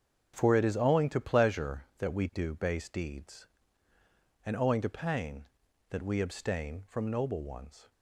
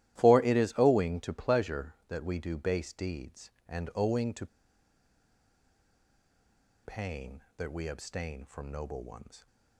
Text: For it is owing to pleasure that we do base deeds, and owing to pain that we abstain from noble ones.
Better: first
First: starts louder than the rest; strong; until 1.3 s; 7.5 dB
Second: starts louder than the rest; strong; until 1.2 s; 14 dB // pauses between "to" and "pain"; strong; at 4.4 s; 2.3 s long

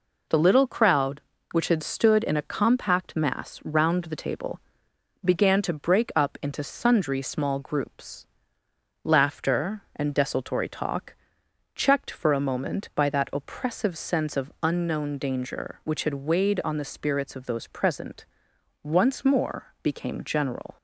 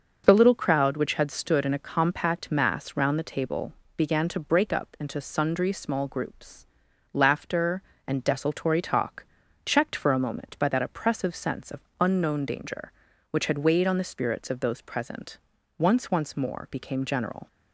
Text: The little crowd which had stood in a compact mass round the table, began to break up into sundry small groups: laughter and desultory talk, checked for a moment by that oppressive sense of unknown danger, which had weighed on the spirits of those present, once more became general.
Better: first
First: none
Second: starts louder than the rest; until 1.2 s; 6.5 dB // pauses between "of" and "unknown"; slight; at 11.8 s; 0.18 s long // says "once" twice; at 16.0 s

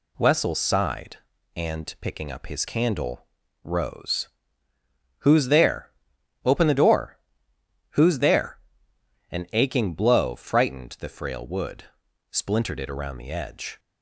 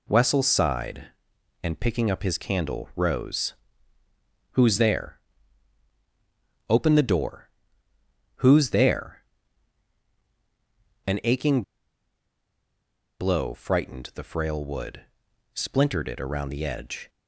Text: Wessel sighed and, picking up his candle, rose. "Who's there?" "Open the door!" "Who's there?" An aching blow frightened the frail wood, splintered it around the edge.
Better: first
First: none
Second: pauses between "aching" and "blow"; strong; at 11.6 s; 1.5 s long

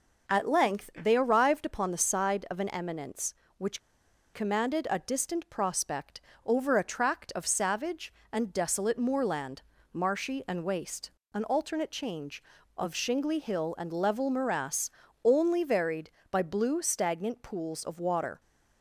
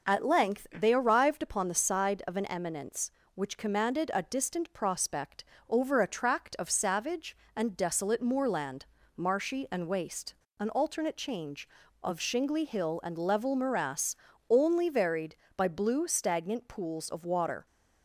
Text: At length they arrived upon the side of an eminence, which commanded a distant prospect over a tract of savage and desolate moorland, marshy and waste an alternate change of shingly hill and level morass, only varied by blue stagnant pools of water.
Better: second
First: pauses between "which" and "commanded"; noticeable; at 3.8 s; 0.53 s long // pauses between "prospect" and "over"; slight; at 6.1 s; 0.24 s long // pauses between "waste" and "an"; slight; at 11.0 s; 0.22 s long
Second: pauses between "prospect" and "over"; slight; at 5.4 s; 0.24 s long // pauses between "waste" and "an"; slight; at 10.3 s; 0.23 s long

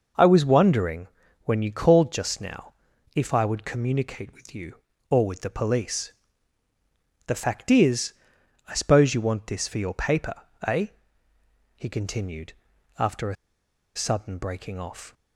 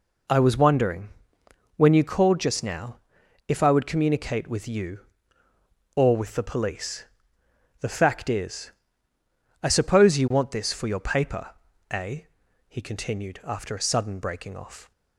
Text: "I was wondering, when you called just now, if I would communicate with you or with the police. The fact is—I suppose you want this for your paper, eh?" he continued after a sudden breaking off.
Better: second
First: pauses between "continued" and "after"; noticeable; at 12.5 s; 0.46 s long // pauses between "a" and "sudden"; noticeable; at 13.3 s; 0.60 s long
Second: none

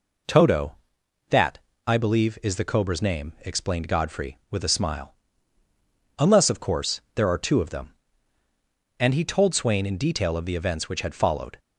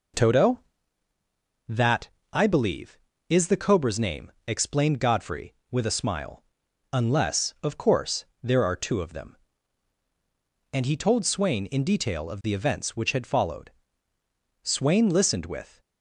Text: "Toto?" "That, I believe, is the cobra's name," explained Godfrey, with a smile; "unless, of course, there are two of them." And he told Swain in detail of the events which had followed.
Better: first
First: none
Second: goes on to say "Swain listened with"; noticeable; from 14.6 s on; 1.1 s long

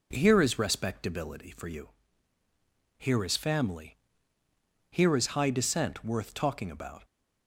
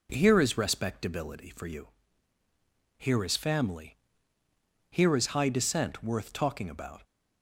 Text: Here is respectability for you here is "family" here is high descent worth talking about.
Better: neither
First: pauses between "you" and "here"; at 1.8 s; 1.0 s long // pauses between "family" and "here"; noticeable; at 3.9 s; 0.96 s long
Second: pauses between "you" and "here"; at 1.8 s; 1.1 s long // pauses between "family" and "here"; noticeable; at 3.9 s; 0.96 s long

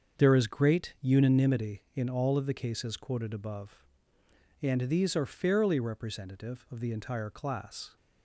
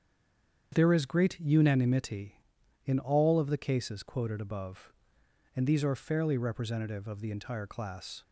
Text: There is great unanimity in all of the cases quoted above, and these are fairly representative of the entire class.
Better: first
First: starts louder than the rest; until 1.2 s; 7 dB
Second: stays silent before the first word; slight; until 0.7 s; 0.7 s long // starts louder than the rest; strong; until 1.7 s; 8 dB

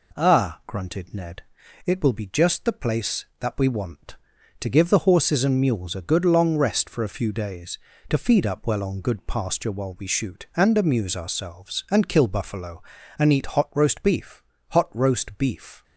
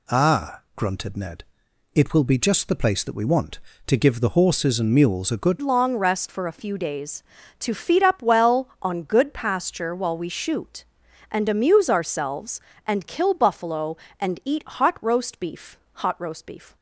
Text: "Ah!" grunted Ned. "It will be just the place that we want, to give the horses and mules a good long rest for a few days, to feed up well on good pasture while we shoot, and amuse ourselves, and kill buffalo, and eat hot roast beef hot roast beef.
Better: first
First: pauses between "beef" and "hot"; slight; at 14.4 s; 0.26 s long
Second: changes voice at "long"; from 5.6 s on; 11.1 s long // pauses between "beef" and "hot"; slight; at 15.7 s; 0.16 s long

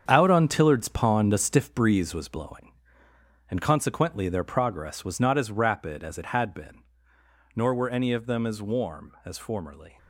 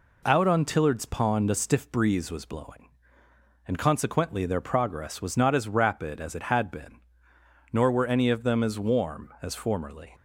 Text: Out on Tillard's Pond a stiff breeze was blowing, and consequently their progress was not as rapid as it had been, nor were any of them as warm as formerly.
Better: second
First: gets quieter; strong; throughout; 10 dB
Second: none

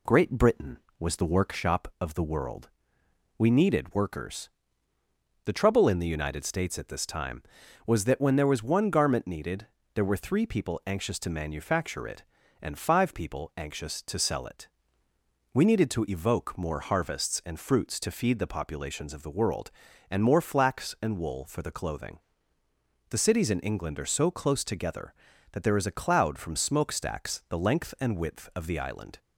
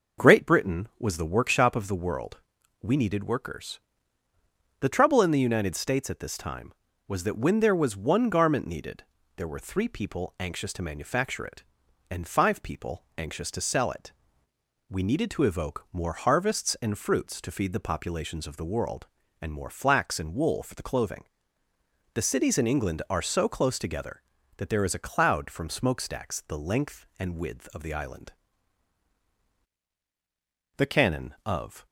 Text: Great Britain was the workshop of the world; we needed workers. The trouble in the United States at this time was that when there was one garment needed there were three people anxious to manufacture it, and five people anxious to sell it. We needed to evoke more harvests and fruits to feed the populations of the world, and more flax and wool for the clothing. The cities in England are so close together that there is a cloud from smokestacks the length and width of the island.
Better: first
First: pauses between "needed" and "there"; slight; at 9.6 s; 0.28 s long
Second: pauses between "needed" and "there"; slight; at 9.0 s; 0.32 s long // goes on to say "The Canon of"; noticeable; from 30.7 s on; 1.0 s long

